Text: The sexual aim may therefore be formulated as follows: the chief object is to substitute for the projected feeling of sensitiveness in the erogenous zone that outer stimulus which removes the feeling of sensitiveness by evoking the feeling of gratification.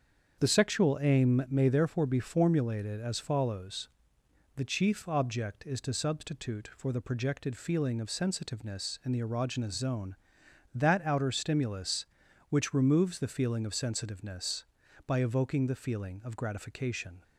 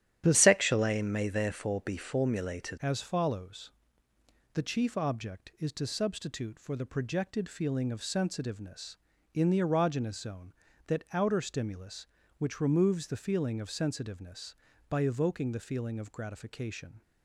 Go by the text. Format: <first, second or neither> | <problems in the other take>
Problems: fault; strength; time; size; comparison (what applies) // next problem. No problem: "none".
first | starts louder than the rest; strong; until 1.2 s; 11.5 dB; strong in the first // changes voice from "sexual" to "formulated"; from 0.3 to 2.7 s; 2.4 s long